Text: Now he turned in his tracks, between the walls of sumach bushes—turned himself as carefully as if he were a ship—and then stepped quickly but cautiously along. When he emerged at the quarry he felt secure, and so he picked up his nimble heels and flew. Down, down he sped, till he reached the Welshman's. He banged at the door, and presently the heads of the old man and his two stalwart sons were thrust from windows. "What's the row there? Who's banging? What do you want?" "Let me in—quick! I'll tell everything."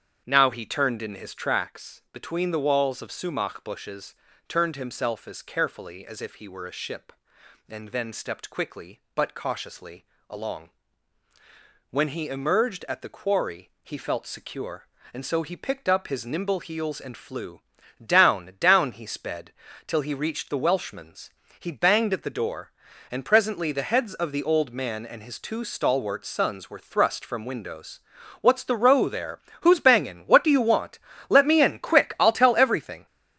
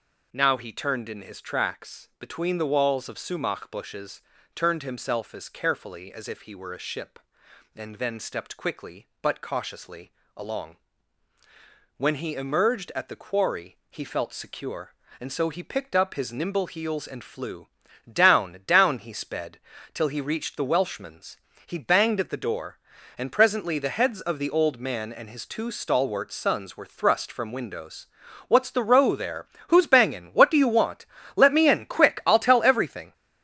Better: second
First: starts louder than the rest; strong; until 1.6 s; 7.5 dB // pauses between "cautiously" and "along"; slight; at 10.0 s; 0.24 s long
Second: pauses between "cautiously" and "along"; slight; at 10.1 s; 0.24 s long

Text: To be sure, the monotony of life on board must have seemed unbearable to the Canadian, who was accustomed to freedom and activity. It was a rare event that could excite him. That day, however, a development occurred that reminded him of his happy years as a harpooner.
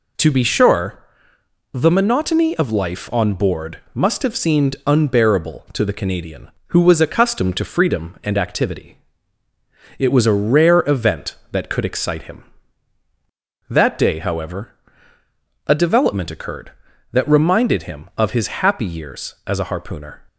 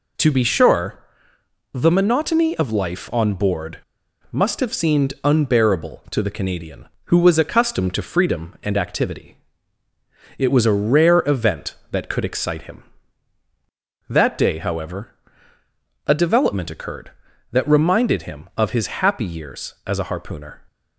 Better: first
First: none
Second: pauses between "board" and "must"; noticeable; at 3.7 s; 0.51 s long

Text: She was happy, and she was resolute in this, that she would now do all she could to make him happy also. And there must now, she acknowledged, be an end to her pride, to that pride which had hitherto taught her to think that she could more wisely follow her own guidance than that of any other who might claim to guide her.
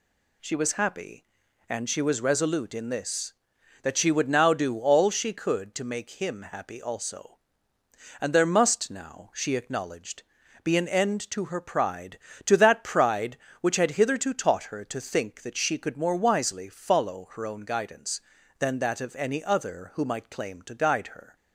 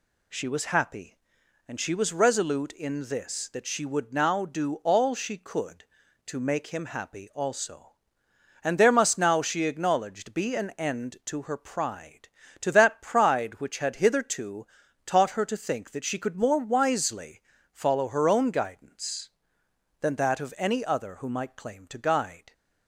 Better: first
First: none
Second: pauses between "hitherto" and "taught"; at 14.6 s; 0.38 s long // pauses between "wisely" and "follow"; slight; at 17.4 s; 0.32 s long // stops before "her"; at 22.5 s

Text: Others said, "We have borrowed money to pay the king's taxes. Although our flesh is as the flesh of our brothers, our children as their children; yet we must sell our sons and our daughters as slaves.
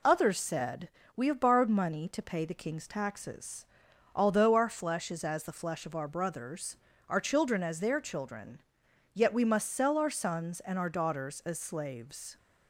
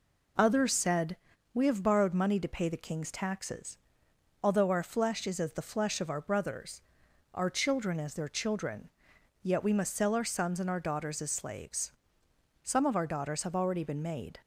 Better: first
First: none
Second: goes on to say "Some of our daughters have already been made"; strong; from 12.6 s on; 1.7 s long

